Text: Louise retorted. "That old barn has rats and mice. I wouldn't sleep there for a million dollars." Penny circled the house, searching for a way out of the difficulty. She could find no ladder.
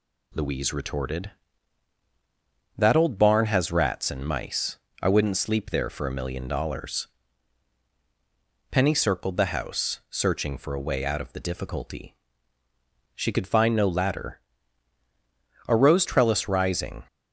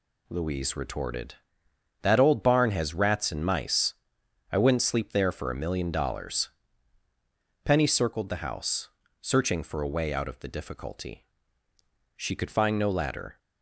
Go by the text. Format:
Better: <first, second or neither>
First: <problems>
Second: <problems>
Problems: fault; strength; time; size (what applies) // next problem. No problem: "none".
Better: second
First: goes on to say "A rose trellis rising"; from 15.6 s on; 1.3 s long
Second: none